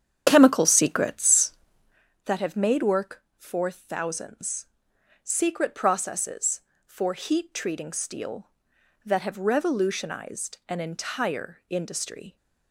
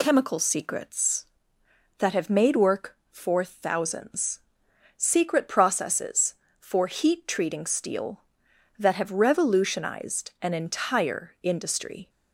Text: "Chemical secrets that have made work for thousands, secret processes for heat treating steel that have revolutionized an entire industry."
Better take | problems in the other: second | starts louder than the rest; strong; until 2.1 s; 8.5 dB

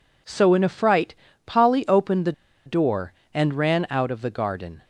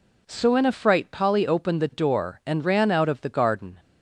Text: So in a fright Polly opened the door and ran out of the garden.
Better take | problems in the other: second | pauses between "fright" and "Polly"; slight; at 1.1 s; 0.30 s long // pauses between "the" and "door"; slight; at 2.3 s; 0.33 s long

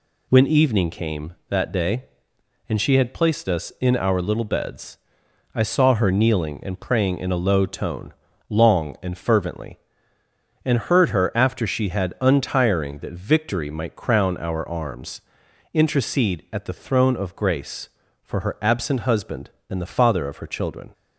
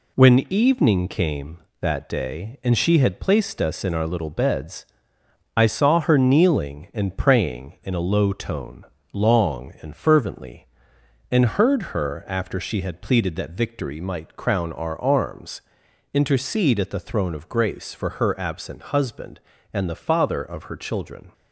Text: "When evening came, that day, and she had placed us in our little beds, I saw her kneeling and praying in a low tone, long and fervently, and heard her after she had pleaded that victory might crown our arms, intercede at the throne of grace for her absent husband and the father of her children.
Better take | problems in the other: second | says "untiring" for "pleaded"; at 12.2 s

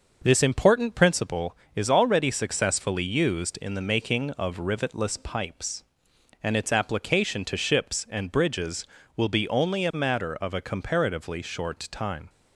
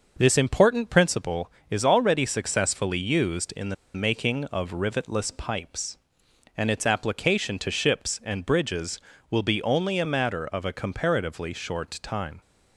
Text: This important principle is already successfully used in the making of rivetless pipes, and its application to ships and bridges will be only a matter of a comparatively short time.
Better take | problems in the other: first | starts louder than the rest; noticeable; until 1.2 s; 6 dB; noticeable in the first // pauses between "the" and "making"; slight; at 3.7 s; 0.19 s long

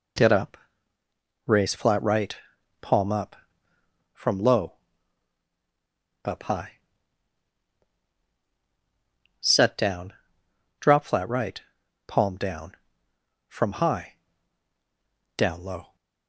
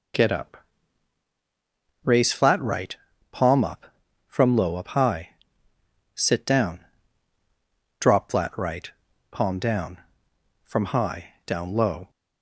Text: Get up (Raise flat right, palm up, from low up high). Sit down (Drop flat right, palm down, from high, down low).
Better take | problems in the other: second | pauses between "low" and "up"; strong; at 4.7 s; 1.5 s long // says "Set" for "Sit"; at 9.3 s

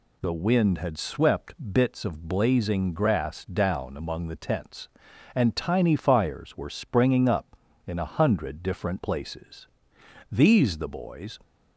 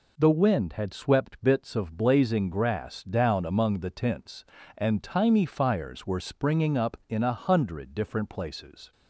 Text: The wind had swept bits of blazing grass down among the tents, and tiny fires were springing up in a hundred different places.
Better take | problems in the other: second | pauses between "swept" and "bits"; slight; at 1.5 s; 0.18 s long // goes on to say "These the boys"; noticeable; from 10.3 s on; 1.0 s long

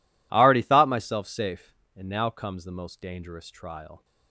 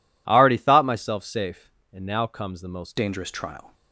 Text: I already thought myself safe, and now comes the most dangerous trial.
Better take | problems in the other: first | changes voice at "dangerous"; from 2.9 s on; 0.8 s long

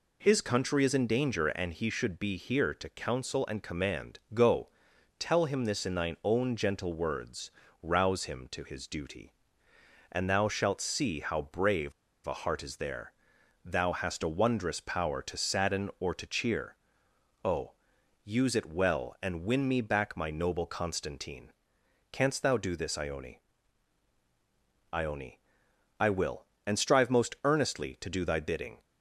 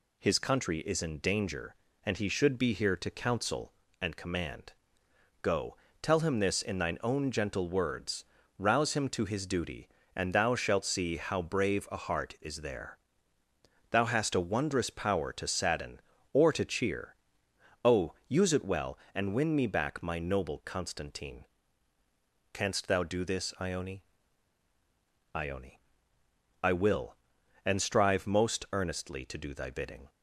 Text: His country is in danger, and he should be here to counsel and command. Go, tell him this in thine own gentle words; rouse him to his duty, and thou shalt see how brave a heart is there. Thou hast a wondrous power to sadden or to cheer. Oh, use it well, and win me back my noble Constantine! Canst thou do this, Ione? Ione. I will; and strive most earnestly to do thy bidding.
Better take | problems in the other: second | pauses between "brave" and "a"; slight; at 11.9 s; 0.34 s long

